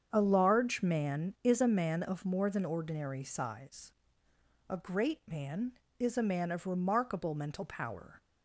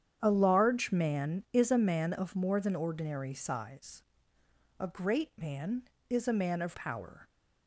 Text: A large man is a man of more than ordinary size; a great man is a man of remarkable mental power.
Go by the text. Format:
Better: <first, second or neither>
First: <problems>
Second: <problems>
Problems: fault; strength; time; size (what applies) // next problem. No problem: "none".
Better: first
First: starts louder than the rest; strong; until 1.1 s; 7.5 dB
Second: starts louder than the rest; strong; until 1.2 s; 9 dB // skips "remarkable mental"; at 6.7 s